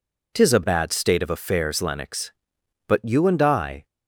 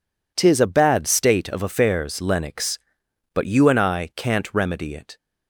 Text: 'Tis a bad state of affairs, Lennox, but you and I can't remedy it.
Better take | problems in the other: second | stops before "can't remedy it"; at 3.8 s

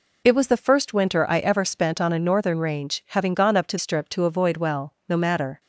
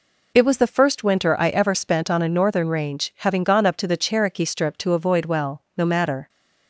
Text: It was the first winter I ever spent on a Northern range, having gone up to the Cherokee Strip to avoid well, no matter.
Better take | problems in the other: second | skips "the Cherokee"; at 3.7 s

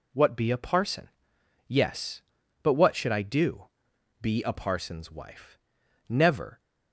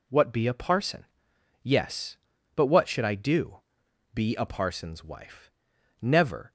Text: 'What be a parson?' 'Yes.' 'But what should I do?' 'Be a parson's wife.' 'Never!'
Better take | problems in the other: neither | none

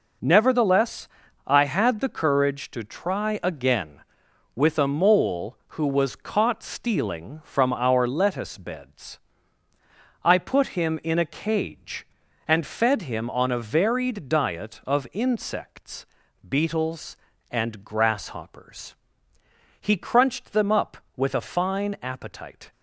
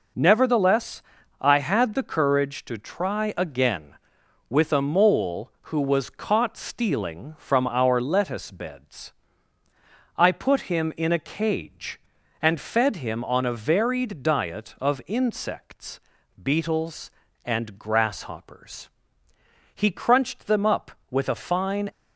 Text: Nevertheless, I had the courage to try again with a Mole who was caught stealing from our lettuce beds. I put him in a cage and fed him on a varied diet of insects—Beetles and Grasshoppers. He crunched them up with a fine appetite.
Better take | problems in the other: first | stops before "appetite"; at 21.8 s

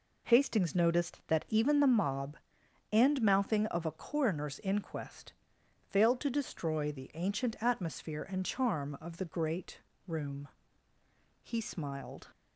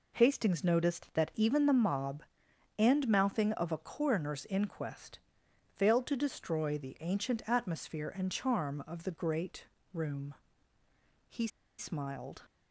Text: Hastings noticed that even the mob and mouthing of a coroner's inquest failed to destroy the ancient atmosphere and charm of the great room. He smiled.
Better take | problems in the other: first | pauses between "inquest" and "failed"; noticeable; at 5.1 s; 0.56 s long; noticeable in the first // pauses between "great" and "room"; slight; at 9.6 s; 0.28 s long; slight in the first // pauses between "He" and "smiled"; slight; at 11.4 s; 0.30 s long

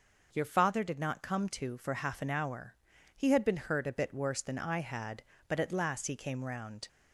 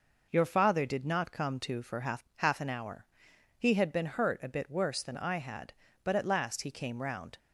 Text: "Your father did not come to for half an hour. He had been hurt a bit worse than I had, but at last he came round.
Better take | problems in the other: first | says "half" twice; at 2.3 s

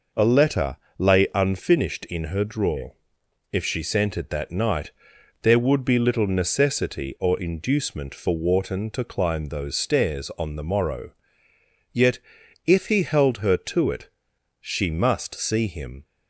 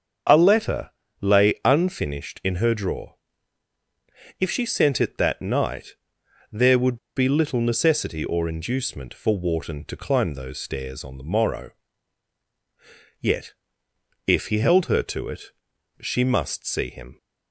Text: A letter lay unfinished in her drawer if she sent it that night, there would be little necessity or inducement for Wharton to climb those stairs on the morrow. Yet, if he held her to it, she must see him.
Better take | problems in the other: first | starts louder than the rest; strong; until 1.7 s; 7.5 dB // pauses between "letter" and "lay"; slight; at 0.8 s; 0.32 s long; slight in the first // pauses between "drawer" and "if"; strong; at 3.1 s; 1.2 s long; noticeable in the first // pauses between "would" and "be"; slight; at 6.9 s; 0.18 s long

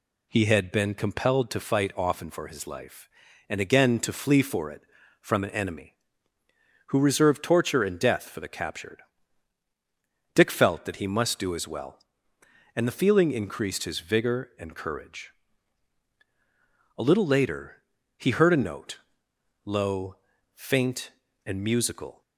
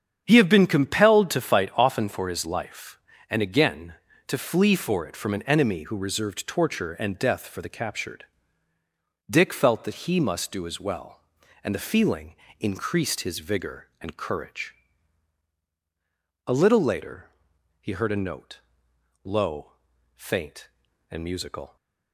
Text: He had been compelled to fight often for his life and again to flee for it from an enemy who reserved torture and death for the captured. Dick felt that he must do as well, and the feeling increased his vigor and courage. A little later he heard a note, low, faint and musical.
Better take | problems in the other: first | starts louder than the rest; strong; until 1.2 s; 8.5 dB // says "have" for "had"; at 0.3 s // pauses between "feeling" and "increased"; slight; at 12.3 s; 0.22 s long // pauses between "later" and "he"; noticeable; at 17.2 s; 0.56 s long; slight in the first

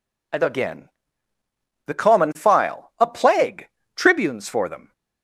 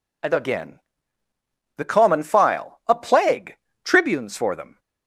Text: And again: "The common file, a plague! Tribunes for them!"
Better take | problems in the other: neither | none

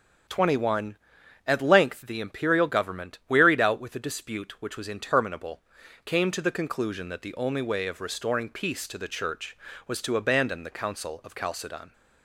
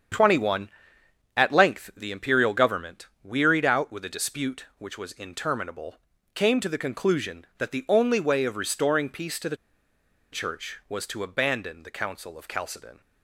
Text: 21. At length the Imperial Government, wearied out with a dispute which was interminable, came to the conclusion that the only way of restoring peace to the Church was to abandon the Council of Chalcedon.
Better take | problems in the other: first | starts louder than the rest; strong; until 1.7 s; 8 dB; strong in the first // pauses between "the" and "Church"; noticeable; at 9.5 s; 0.75 s long

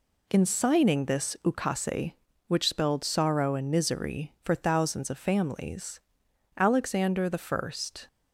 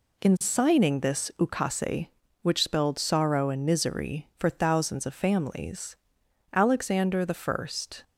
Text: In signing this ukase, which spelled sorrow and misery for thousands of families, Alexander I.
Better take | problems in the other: neither | none

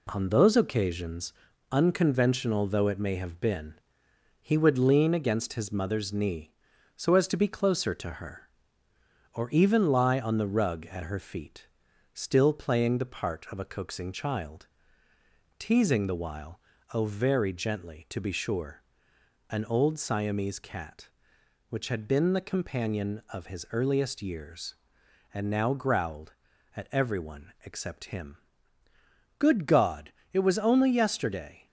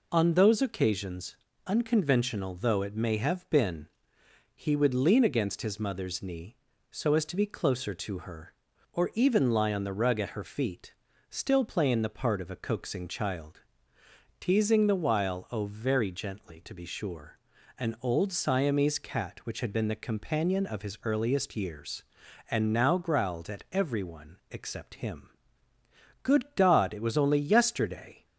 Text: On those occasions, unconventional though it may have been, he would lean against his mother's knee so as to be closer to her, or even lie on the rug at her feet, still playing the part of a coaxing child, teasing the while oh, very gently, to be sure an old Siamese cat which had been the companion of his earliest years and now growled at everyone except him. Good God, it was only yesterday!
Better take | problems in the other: second | gets quieter; noticeable; throughout; 4 dB // pauses between "while" and "oh"; slight; at 16.5 s; 0.34 s long // pauses between "sure" and "an"; noticeable; at 18.8 s; 0.66 s long; also in the second

